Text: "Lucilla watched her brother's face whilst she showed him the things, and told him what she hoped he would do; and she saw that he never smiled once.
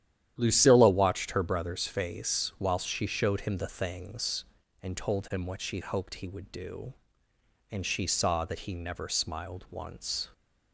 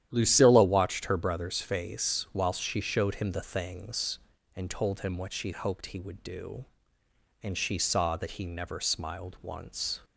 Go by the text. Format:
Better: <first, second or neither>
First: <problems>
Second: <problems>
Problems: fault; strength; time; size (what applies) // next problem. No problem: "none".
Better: neither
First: starts louder than the rest; strong; until 1.3 s; 11 dB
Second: starts louder than the rest; strong; until 1.1 s; 11 dB